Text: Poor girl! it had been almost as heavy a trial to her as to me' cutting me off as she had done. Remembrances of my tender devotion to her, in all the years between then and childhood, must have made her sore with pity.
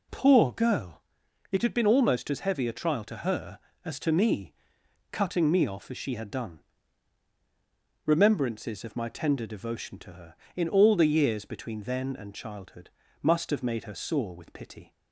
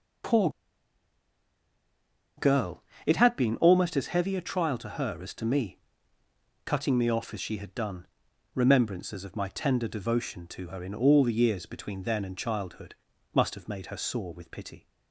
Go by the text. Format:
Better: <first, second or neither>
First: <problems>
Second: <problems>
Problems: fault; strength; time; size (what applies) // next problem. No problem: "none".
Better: first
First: pauses between "me" and "cutting"; noticeable; at 4.5 s; 0.58 s long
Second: pauses between "Poor" and "girl"; strong; at 0.4 s; 1.8 s long // pauses between "me" and "cutting"; noticeable; at 5.7 s; 0.86 s long